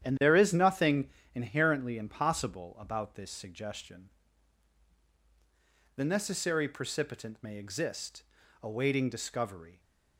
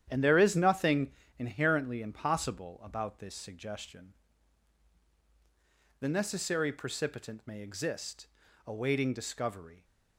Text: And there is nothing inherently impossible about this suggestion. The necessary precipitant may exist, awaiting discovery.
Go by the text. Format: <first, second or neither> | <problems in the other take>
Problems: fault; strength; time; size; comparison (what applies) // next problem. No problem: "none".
neither | starts louder than the rest; strong; the same in both // pauses between "nothing" and "inherently"; slight; the same in both